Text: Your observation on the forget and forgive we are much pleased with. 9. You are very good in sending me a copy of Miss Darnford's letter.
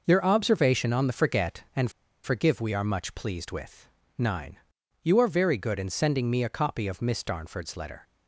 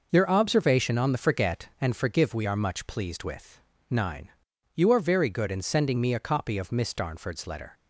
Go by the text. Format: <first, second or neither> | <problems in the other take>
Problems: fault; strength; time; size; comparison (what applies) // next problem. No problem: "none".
second | pauses between "and" and "forgive"; slight; at 1.9 s; 0.33 s long